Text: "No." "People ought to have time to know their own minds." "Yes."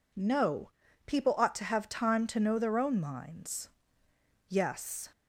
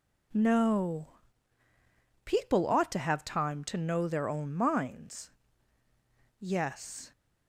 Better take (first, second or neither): neither